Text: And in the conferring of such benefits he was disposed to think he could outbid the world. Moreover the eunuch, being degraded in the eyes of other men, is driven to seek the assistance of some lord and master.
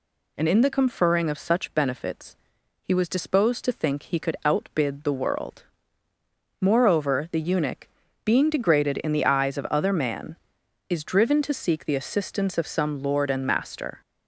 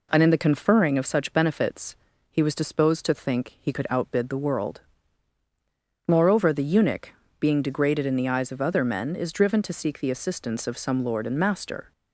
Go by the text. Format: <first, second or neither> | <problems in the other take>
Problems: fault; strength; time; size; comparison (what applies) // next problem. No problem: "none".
second | pauses between "benefits" and "he"; noticeable; at 2.3 s; 0.46 s long; slight in the second // says "man" for "men"; at 9.9 s